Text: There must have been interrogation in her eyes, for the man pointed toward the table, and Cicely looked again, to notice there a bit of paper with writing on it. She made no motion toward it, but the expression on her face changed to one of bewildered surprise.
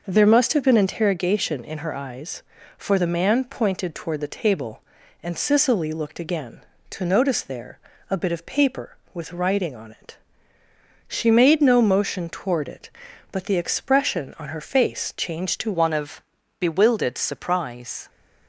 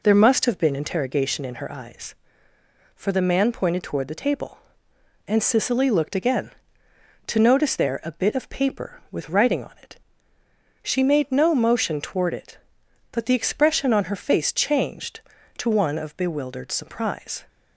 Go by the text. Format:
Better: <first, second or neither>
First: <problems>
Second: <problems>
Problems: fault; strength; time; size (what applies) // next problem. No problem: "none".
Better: second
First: pauses between "there" and "a"; slight; at 7.7 s; 0.32 s long // changes voice at "one"; from 15.7 s on; 2.3 s long // pauses between "of" and "bewildered"; at 16.2 s; 0.38 s long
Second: none